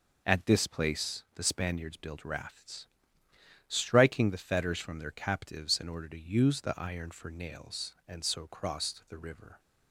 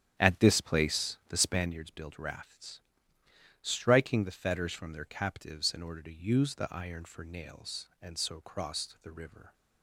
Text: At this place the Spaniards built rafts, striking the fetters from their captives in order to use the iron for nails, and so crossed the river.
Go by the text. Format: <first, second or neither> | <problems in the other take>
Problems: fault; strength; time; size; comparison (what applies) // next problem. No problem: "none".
first | starts louder than the rest; strong; until 1.7 s; 9.5 dB